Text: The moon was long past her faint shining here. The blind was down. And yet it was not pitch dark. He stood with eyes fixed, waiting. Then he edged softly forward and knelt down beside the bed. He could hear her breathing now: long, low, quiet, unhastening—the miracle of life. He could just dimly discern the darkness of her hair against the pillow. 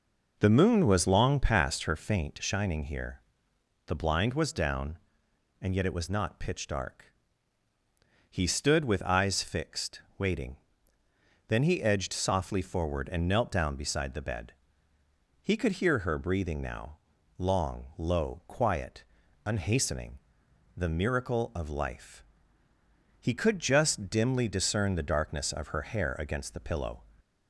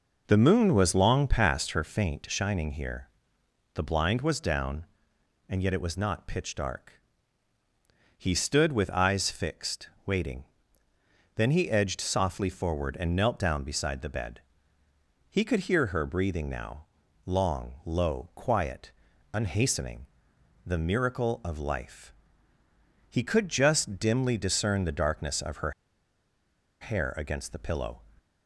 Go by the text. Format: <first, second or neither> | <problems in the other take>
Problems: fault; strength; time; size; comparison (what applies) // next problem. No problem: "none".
first | pauses between "her" and "hair"; at 25.7 s; 1.0 s long